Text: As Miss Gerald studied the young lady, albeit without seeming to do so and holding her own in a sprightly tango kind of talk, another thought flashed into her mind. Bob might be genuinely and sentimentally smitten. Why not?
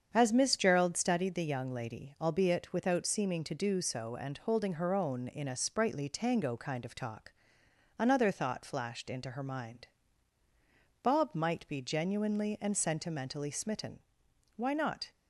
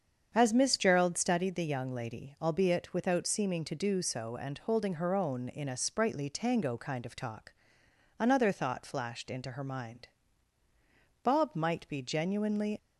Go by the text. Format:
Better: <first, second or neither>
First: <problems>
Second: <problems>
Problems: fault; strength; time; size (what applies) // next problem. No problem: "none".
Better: first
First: starts louder than the rest; strong; until 1.1 s; 7.5 dB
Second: starts louder than the rest; strong; until 1.3 s; 7.5 dB // stops before "and sentimentally smitten Why not"; at 12.7 s